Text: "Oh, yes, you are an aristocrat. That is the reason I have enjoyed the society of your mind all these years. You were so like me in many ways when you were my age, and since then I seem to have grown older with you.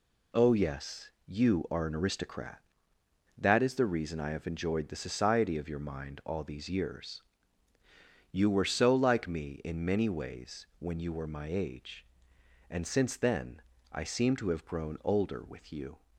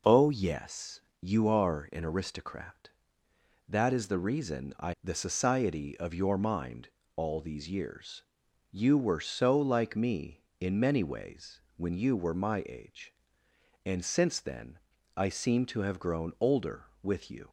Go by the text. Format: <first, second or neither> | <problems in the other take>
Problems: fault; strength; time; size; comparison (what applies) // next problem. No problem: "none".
first | skips "have enjoyed"; at 4.9 s // pauses between "mind" and "all"; slight; at 6.8 s; 0.26 s long // pauses between "ways" and "when"; slight; at 11.6 s; 0.16 s long // pauses between "then" and "I"; at 14.7 s; 0.40 s long; slight in the first